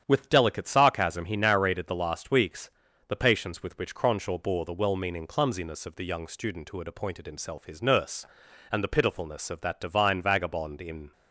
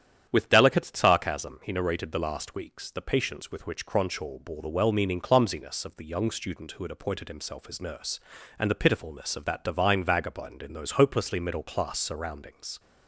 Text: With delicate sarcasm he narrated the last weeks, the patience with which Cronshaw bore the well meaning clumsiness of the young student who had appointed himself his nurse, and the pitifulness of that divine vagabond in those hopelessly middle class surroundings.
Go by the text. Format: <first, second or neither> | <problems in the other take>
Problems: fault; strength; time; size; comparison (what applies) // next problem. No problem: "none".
second | starts louder than the rest; strong; until 1.0 s; 9 dB; strong in the second // stops before "those hopelessly middle class surroundings"; at 11.1 s